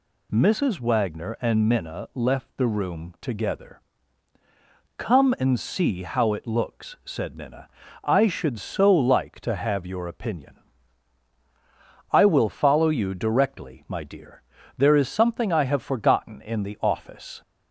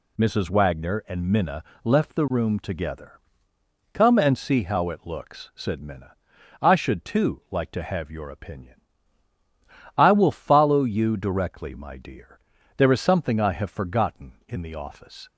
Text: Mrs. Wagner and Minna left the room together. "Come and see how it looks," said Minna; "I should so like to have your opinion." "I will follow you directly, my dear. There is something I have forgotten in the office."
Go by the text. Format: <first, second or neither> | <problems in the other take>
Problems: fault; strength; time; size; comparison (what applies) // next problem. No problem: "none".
first | pauses between "Minna" and "left"; slight; at 1.6 s; 0.22 s long // says "too" for "so"; at 7.0 s